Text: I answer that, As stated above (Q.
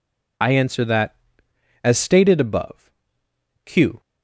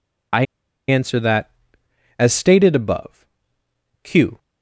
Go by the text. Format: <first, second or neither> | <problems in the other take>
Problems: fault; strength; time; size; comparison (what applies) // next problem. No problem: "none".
first | pauses between "I" and "answer"; at 0.4 s; 0.45 s long